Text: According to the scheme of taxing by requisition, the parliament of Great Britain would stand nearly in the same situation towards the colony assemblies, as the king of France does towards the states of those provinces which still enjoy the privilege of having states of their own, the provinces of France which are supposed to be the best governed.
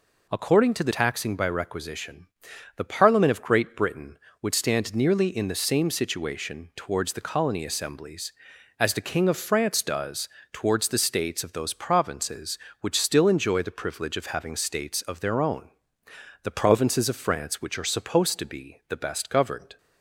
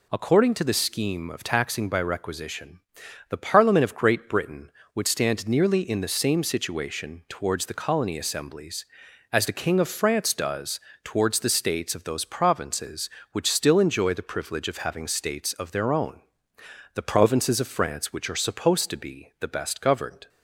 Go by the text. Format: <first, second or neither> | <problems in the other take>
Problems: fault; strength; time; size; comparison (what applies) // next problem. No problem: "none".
second | skips "scheme of"; at 0.9 s // pauses between "does" and "towards"; slight; at 10.2 s; 0.24 s long; slight in the second